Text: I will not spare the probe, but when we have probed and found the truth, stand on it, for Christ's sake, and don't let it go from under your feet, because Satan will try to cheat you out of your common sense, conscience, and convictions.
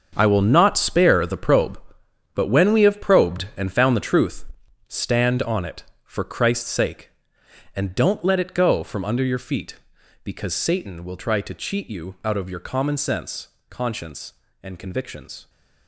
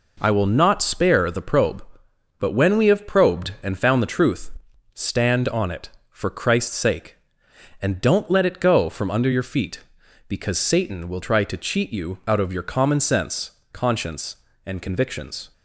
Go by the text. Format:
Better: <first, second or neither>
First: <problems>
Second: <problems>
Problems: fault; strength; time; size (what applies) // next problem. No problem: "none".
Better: second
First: gets quieter; strong; throughout; 12.5 dB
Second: none